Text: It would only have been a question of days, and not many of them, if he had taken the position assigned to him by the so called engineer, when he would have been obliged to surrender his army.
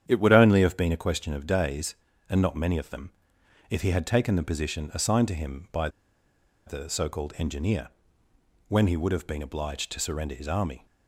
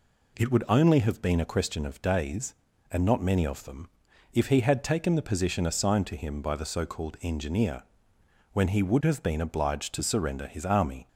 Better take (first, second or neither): second